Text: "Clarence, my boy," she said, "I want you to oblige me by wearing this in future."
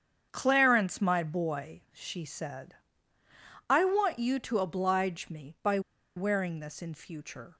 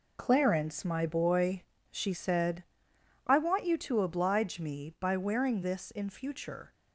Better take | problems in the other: second | starts louder than the rest; strong; until 1.3 s; 7.5 dB // pauses between "by" and "wearing"; at 5.7 s; 0.36 s long

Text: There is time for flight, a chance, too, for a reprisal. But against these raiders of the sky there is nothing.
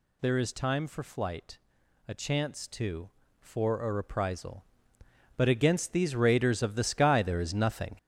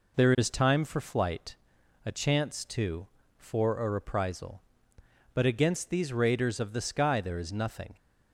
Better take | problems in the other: second | gets louder; strong; throughout; 8 dB

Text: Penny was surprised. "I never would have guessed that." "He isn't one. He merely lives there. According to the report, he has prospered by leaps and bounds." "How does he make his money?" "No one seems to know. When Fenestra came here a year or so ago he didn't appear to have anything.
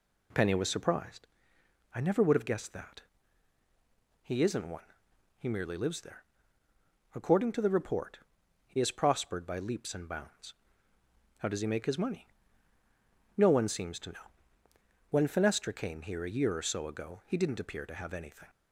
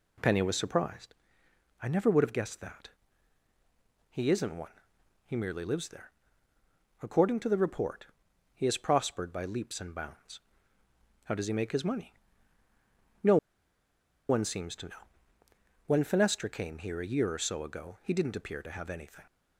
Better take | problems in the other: first | pauses between "No" and "one"; noticeable; at 13.3 s; 0.92 s long

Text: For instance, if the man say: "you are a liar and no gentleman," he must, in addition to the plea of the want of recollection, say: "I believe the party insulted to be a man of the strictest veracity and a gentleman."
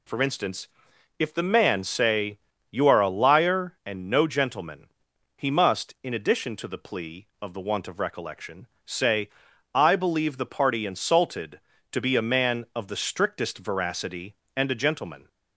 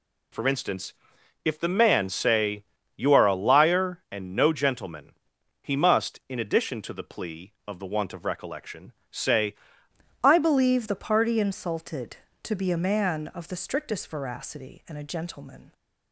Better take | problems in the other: first | changes voice at "I"; from 10.2 s on; 5.5 s long

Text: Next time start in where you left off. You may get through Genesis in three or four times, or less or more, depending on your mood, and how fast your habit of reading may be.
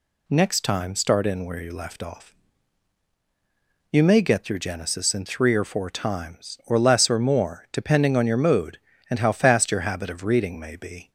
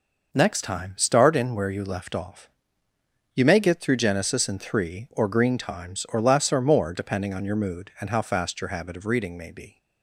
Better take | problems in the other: first | says "green" for "four"; at 5.2 s

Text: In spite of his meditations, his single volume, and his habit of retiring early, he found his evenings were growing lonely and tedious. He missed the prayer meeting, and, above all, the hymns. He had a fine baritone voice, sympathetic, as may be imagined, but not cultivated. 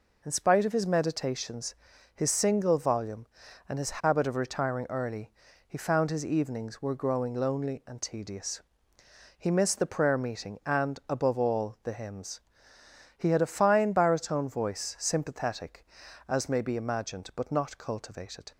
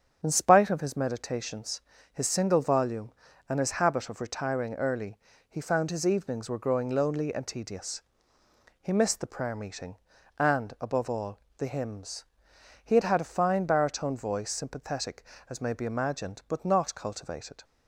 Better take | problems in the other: first | starts louder than the rest; strong; until 1.2 s; 8 dB // says "had" twice; at 13.0 s

